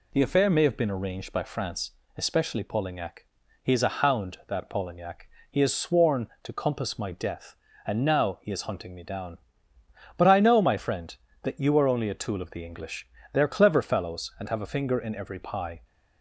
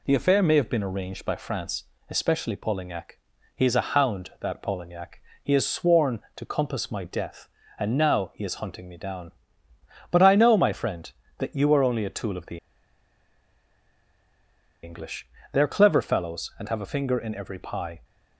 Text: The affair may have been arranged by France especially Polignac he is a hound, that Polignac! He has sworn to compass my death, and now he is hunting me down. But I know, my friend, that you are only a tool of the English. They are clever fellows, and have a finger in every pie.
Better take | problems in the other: first | pauses between "France" and "especially"; slight; at 1.8 s; 0.24 s long; slight in the first // pauses between "Polignac" and "he"; slight; at 3.1 s; 0.36 s long; slight in the first // pauses between "the" and "English"; strong; at 12.5 s; 2.2 s long

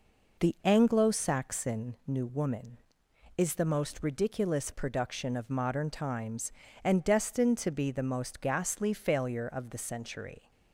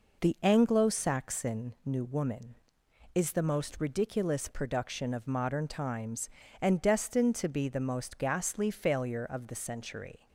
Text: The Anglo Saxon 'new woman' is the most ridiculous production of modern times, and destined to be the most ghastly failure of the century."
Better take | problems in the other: neither | none

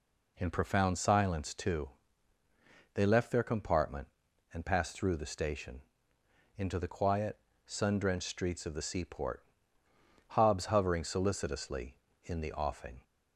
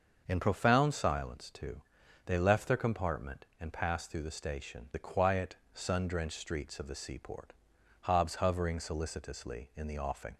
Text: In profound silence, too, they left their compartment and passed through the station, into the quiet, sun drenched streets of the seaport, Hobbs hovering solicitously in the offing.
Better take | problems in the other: first | starts louder than the rest; until 1.2 s; 6 dB // skips "into"; at 4.9 s

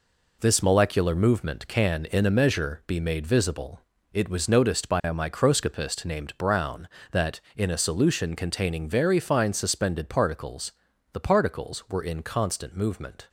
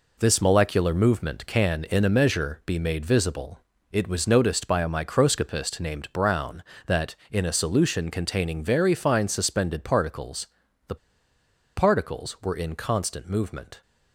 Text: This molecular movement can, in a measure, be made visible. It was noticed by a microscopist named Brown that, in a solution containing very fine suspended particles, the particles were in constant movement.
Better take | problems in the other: first | pauses between "the" and "particles"; noticeable; at 10.9 s; 0.80 s long

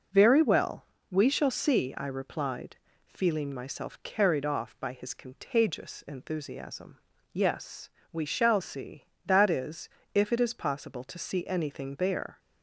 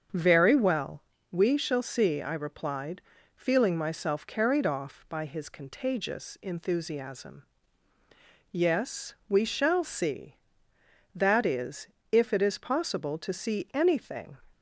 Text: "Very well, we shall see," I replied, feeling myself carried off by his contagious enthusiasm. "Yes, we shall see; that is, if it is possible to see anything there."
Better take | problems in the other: first | starts louder than the rest; until 1.4 s; 7 dB // stops before "there"; at 14.5 s

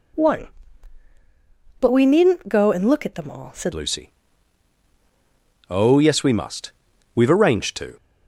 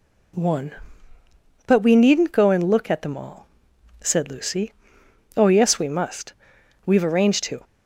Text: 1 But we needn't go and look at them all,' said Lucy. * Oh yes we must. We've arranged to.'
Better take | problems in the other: second | changes voice at "Lucy"; from 3.7 s on; 4.2 s long

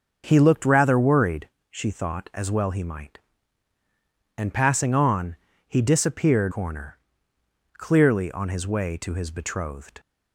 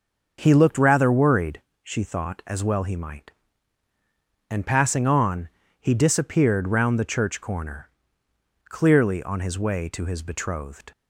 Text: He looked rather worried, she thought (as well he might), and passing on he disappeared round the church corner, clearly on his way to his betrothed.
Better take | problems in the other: second | starts louder than the rest; until 1.2 s; 6.5 dB; also in the second // pauses between "on" and "he"; slight; at 5.3 s; 0.30 s long; slight in the second // skips "round the church"; at 6.5 s

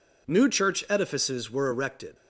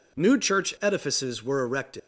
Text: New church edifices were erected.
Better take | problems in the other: first | leaves "erected" unfinished; at 1.9 s; 80 ms

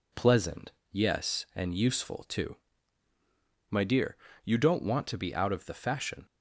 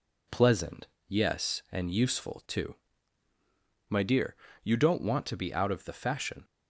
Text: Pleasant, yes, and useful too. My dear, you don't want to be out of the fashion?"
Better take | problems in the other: neither | none

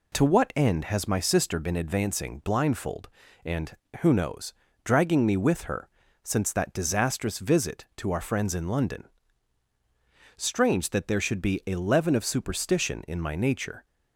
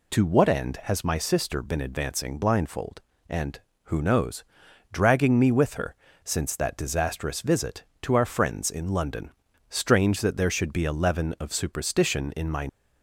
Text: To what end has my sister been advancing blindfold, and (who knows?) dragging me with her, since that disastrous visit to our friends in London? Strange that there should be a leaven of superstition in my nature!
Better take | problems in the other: first | stops before "nature"; at 12.6 s

